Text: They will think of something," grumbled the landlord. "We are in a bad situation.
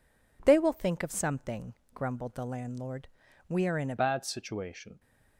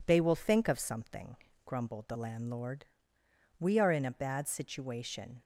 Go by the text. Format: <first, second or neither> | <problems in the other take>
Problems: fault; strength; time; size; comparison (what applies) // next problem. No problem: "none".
second | changes voice at "bad"; from 3.9 s on; 1.0 s long